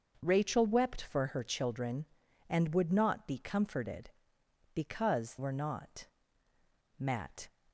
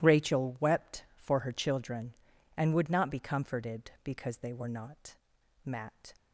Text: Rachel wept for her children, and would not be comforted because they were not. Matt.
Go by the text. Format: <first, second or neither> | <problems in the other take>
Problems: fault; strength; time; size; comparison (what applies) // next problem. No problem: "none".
second | starts louder than the rest; noticeable; until 1.2 s; 6 dB // skips "they"; at 5.3 s